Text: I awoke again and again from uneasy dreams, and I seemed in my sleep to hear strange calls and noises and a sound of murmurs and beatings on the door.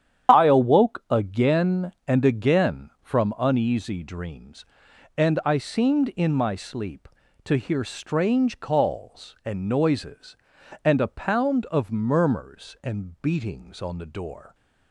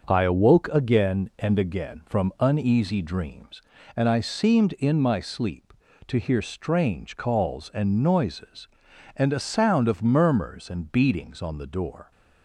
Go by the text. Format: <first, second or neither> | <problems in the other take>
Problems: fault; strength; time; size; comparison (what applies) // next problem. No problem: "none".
second | starts louder than the rest; strong; until 1.3 s; 9 dB; also in the second // says "pound" for "sound"; at 11.0 s